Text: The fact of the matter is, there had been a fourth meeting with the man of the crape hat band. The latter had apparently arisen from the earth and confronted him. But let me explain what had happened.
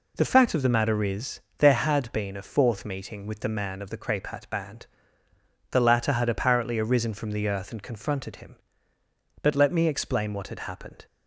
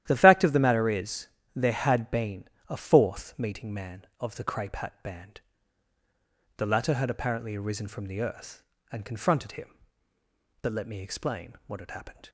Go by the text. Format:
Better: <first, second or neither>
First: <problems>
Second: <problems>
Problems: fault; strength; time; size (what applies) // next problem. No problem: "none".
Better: first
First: none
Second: starts louder than the rest; strong; until 1.0 s; 12 dB // pauses between "been" and "a"; slight; at 2.4 s; 0.22 s long // skips "with the"; at 3.7 s